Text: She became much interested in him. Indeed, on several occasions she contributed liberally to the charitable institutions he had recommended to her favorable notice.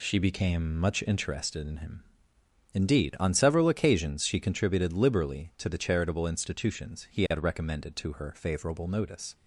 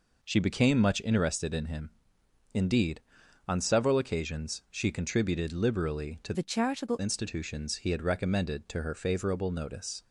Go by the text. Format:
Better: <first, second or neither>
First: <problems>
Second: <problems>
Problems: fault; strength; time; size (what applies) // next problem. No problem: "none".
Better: first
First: none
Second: changes voice from "the" to "charitable"; from 6.3 to 7.0 s; 0.7 s long